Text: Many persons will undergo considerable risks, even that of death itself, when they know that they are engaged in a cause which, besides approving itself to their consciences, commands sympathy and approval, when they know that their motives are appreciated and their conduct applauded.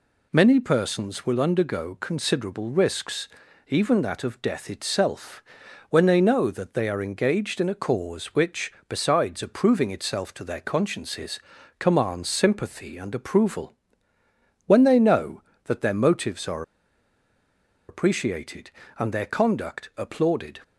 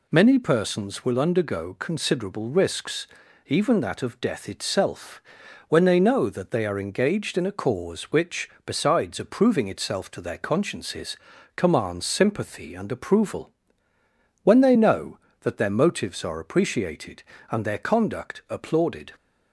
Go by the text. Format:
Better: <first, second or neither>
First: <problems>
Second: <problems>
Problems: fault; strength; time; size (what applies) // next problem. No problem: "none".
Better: second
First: pauses between "are" and "appreciated"; strong; at 16.6 s; 1.2 s long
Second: none